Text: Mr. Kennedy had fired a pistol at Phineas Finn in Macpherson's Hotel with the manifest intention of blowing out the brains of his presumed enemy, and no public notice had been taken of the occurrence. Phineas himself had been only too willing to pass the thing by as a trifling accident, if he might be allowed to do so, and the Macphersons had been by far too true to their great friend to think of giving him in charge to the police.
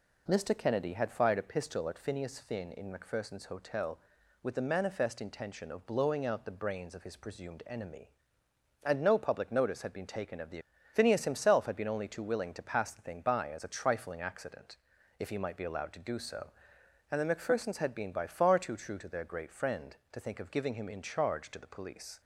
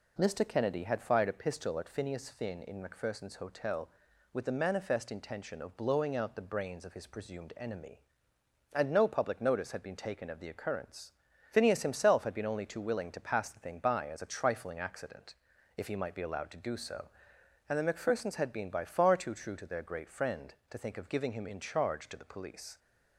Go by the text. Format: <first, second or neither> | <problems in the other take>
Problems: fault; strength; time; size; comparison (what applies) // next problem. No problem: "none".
second | skips "occurrence"; at 10.7 s